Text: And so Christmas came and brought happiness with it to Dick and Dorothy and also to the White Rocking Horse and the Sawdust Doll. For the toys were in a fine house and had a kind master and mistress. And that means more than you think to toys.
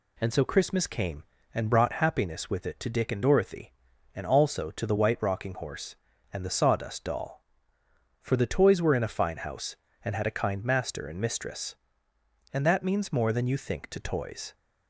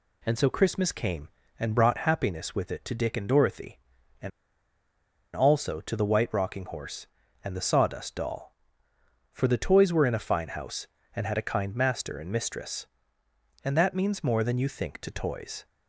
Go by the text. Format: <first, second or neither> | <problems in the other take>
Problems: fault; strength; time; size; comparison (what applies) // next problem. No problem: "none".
first | pauses between "and" and "also"; at 4.3 s; 1.0 s long